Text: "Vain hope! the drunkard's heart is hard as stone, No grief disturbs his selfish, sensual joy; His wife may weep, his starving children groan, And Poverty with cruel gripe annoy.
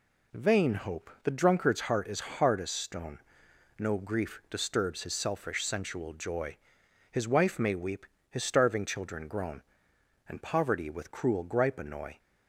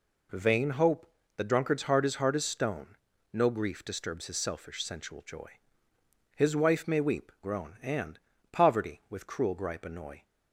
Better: first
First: none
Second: skips "his starving children"; at 7.3 s // pauses between "And" and "Poverty"; slight; at 8.1 s; 0.32 s long

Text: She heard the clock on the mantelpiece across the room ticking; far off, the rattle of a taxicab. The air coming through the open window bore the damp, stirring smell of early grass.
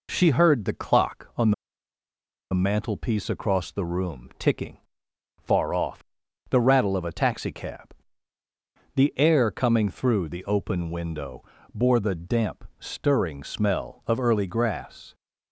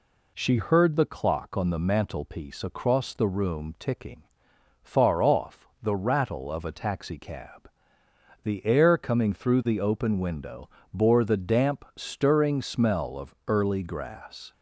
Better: second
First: pauses between "on" and "the"; at 1.5 s; 0.99 s long // pauses between "window" and "bore"; slight; at 11.4 s; 0.28 s long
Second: pauses between "window" and "bore"; slight; at 10.6 s; 0.24 s long

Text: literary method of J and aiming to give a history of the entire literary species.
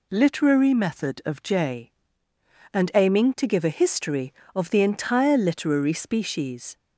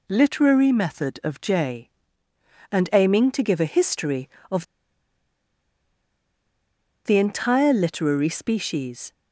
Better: first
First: none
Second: pauses between "of" and "the"; strong; at 4.6 s; 2.4 s long

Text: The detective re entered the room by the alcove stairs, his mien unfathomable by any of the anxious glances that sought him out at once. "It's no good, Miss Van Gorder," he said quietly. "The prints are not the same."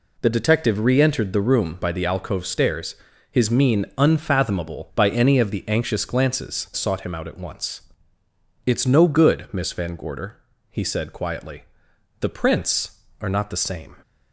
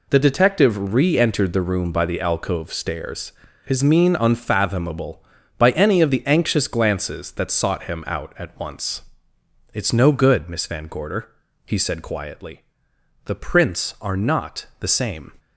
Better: second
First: skips "that"; at 6.7 s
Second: none

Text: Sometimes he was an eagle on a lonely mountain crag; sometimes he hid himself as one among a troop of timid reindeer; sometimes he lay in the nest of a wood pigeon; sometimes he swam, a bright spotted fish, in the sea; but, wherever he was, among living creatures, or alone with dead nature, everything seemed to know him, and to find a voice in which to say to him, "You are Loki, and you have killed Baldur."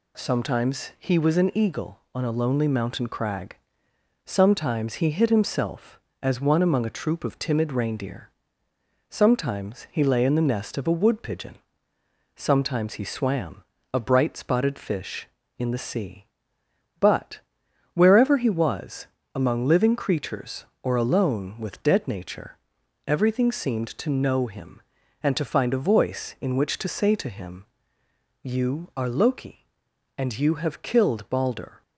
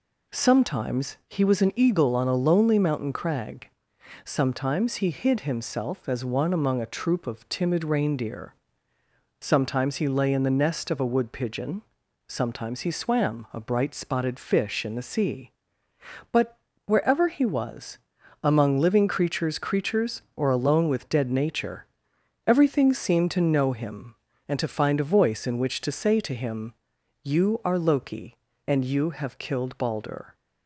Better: first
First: none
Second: says "creatures" twice; at 19.5 s

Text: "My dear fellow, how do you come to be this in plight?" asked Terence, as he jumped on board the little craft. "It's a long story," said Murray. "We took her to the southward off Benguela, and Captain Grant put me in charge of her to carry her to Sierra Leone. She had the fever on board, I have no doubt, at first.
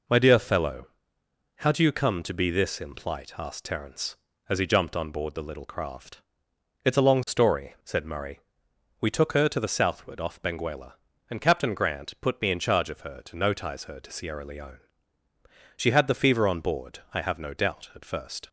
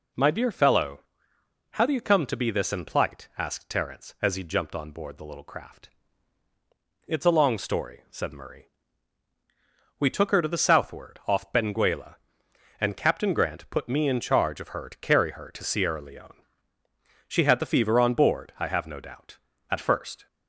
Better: second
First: says "notize" for "carry"; at 13.3 s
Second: none

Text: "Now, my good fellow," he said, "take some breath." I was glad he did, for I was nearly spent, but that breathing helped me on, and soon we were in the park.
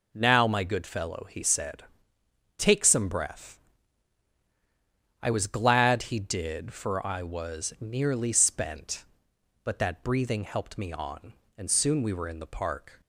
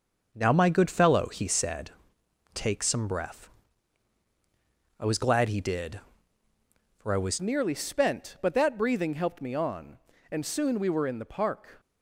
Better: first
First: none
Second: starts louder than the rest; until 1.3 s; 6.5 dB // changes voice at "nearly"; from 7.3 s on; 4.4 s long

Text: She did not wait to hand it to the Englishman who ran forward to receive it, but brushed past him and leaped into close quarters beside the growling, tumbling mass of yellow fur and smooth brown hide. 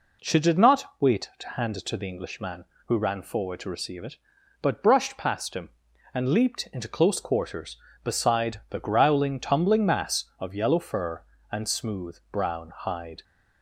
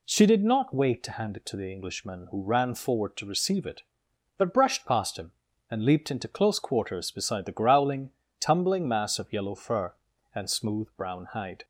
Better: neither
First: none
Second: none

